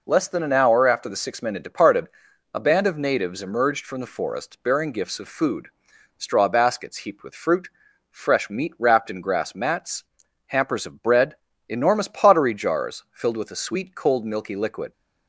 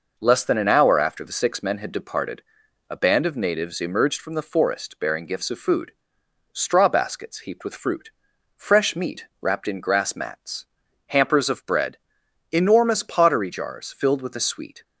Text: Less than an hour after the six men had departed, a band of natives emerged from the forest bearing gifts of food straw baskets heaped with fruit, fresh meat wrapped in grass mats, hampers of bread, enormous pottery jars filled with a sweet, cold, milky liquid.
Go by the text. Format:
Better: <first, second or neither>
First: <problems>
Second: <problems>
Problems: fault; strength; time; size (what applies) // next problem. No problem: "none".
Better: first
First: pauses between "food" and "straw"; noticeable; at 5.6 s; 0.50 s long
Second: pauses between "food" and "straw"; noticeable; at 5.9 s; 0.62 s long // pauses between "meat" and "wrapped"; slight; at 9.2 s; 0.16 s long // stops before "cold milky liquid"; at 14.8 s